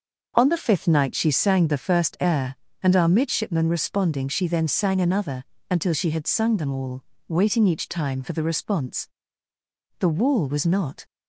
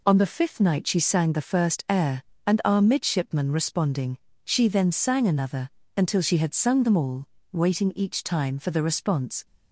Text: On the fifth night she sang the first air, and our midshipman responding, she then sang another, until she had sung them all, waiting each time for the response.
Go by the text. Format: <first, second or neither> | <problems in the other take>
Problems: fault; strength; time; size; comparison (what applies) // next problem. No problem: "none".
second | goes on to say "The wall was not"; noticeable; from 9.9 s on; 1.0 s long